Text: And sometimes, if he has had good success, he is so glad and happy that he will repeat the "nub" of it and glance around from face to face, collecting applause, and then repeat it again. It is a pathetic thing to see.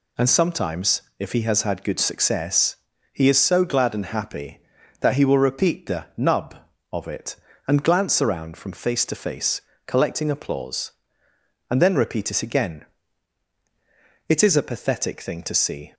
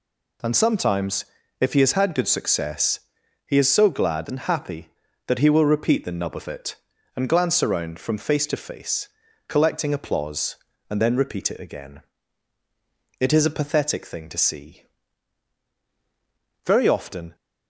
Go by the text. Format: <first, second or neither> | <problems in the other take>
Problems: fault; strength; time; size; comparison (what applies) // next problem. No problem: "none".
first | goes on to say "Very often"; noticeable; from 16.6 s on; 0.70 s long